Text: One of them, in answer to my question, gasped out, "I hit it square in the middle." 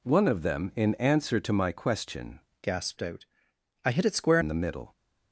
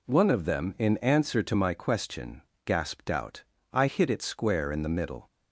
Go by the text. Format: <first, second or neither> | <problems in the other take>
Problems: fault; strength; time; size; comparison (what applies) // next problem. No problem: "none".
second | changes voice from "gasped" to "square"; from 2.6 to 4.3 s; 1.7 s long